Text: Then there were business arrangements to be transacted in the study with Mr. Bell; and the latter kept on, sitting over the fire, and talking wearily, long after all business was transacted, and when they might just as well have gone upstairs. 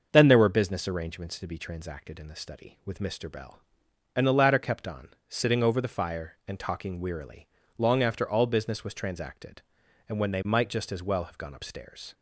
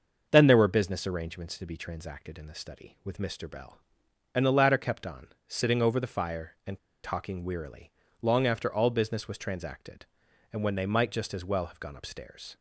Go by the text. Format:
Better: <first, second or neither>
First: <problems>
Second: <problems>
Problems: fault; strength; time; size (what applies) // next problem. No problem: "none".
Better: first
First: starts louder than the rest; until 1.1 s; 6 dB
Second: starts louder than the rest; until 1.3 s; 6 dB // pauses between "and" and "talking"; slight; at 6.7 s; 0.27 s long